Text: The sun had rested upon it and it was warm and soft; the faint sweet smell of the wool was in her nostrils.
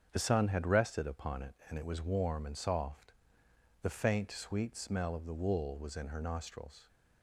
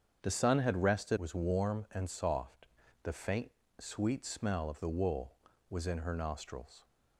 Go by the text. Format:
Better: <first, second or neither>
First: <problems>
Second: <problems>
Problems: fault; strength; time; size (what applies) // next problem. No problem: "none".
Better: first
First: starts louder than the rest; strong; until 1.1 s; 7.5 dB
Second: starts louder than the rest; strong; until 1.2 s; 7.5 dB // skips "upon it and it"; at 1.1 s // pauses between "faint" and "sweet"; slight; at 3.5 s; 0.30 s long